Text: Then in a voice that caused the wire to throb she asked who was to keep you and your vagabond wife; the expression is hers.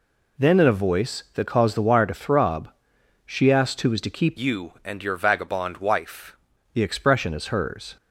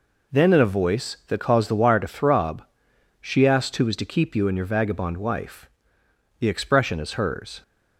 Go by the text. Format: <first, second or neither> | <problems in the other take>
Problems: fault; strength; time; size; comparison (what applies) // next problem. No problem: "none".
second | pauses between "throb" and "she"; noticeable; at 2.6 s; 0.54 s long; noticeable in the second // changes voice from "you" to "wife"; from 4.3 to 6.3 s; 2.0 s long